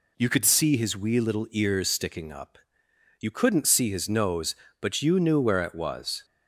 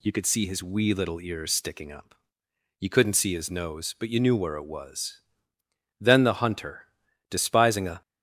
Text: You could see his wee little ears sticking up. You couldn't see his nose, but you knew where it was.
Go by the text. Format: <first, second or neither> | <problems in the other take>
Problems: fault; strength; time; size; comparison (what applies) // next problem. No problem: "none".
first | goes on to say "Then the hunter despising a"; strong; from 5.9 s on; 2.0 s long